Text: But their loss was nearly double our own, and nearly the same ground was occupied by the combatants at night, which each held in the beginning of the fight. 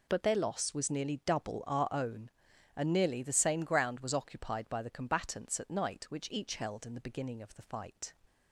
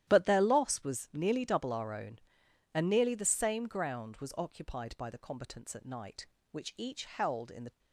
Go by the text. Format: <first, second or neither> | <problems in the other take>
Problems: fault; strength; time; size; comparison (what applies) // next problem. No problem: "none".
first | starts louder than the rest; strong; until 1.0 s; 12 dB // stops before "beginning of the fight"; at 7.7 s